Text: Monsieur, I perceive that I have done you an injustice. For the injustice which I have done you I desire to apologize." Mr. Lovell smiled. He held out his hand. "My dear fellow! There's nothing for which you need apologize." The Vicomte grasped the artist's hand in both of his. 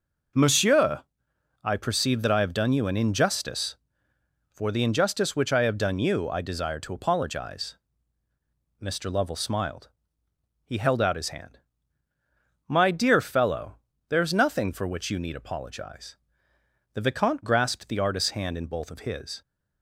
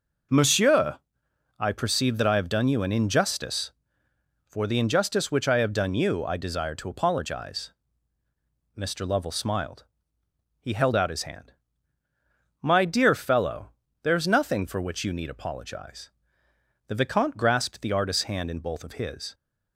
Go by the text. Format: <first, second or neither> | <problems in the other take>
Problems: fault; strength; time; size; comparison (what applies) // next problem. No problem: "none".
neither | none